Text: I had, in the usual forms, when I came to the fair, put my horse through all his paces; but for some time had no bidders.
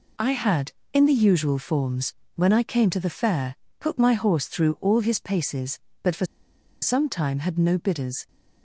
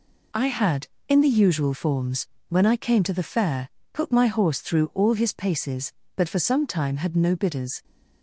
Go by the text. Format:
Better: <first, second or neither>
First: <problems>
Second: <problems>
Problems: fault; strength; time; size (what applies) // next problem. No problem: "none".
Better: second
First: pauses between "for" and "some"; noticeable; at 6.2 s; 0.56 s long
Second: none